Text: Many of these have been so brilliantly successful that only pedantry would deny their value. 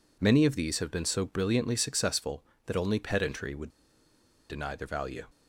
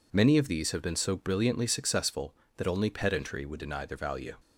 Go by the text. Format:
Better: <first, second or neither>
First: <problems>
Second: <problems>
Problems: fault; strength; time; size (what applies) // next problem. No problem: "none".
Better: second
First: pauses between "would" and "deny"; noticeable; at 3.6 s; 0.81 s long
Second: none